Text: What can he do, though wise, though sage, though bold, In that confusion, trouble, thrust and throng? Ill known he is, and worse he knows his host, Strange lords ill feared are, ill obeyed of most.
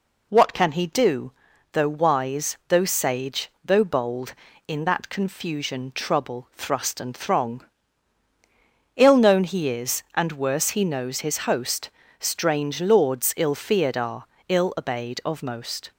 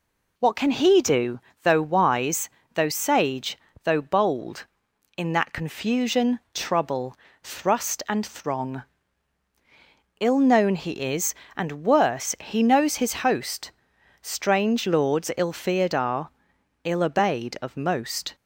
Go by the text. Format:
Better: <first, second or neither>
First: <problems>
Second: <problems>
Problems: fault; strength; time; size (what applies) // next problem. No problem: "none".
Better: neither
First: none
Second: none